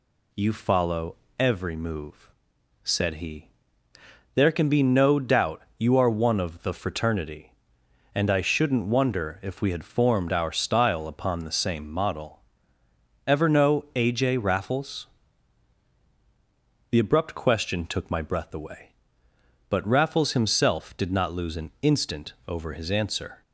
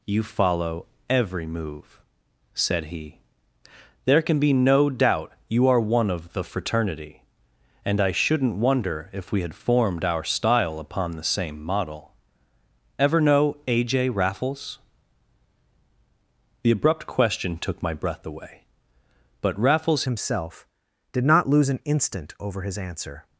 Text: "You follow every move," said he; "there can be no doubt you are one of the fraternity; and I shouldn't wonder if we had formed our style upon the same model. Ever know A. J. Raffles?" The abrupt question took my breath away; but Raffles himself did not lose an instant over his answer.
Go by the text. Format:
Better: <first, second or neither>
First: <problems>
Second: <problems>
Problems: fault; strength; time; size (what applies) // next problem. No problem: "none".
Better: first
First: pauses between "follow" and "every"; slight; at 1.1 s; 0.22 s long // pauses between "doubt" and "you"; slight; at 5.6 s; 0.16 s long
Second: pauses between "follow" and "every"; slight; at 0.8 s; 0.22 s long // pauses between "doubt" and "you"; slight; at 5.3 s; 0.16 s long // changes voice at "himself"; from 20.0 s on; 3.2 s long